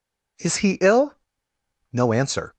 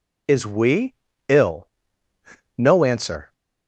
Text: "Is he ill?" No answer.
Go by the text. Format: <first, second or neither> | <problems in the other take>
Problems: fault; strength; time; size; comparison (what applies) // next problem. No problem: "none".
first | says "we" for "he"; at 0.4 s